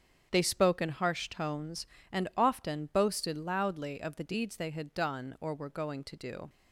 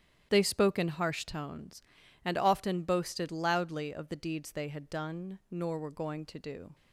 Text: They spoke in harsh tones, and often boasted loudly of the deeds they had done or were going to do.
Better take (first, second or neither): first